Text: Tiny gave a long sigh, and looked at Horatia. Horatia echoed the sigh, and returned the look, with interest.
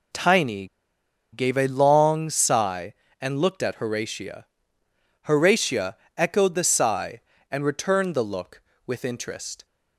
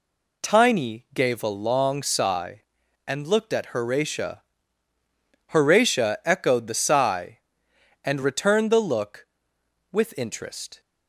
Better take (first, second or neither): second